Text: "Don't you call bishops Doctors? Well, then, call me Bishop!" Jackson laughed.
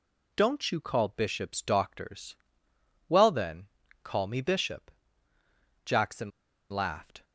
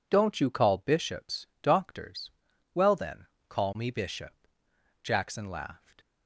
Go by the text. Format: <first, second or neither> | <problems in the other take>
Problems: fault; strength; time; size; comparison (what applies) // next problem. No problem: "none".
second | pauses between "Jackson" and "laughed"; at 6.2 s; 0.40 s long